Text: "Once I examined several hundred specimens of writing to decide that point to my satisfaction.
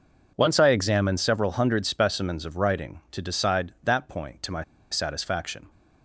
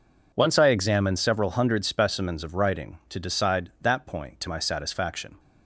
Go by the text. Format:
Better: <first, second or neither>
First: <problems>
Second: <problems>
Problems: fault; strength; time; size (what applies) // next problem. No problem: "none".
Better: second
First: pauses between "my" and "satisfaction"; slight; at 4.6 s; 0.28 s long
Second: none